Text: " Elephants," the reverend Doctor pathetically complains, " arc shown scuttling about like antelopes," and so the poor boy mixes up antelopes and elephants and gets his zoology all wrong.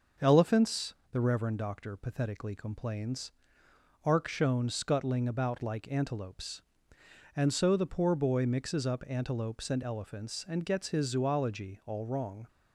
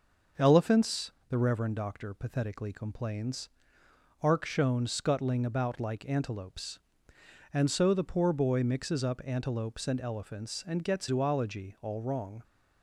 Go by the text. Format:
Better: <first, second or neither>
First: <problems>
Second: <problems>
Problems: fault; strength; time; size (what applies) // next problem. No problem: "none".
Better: first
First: none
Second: skips "his"; at 11.0 s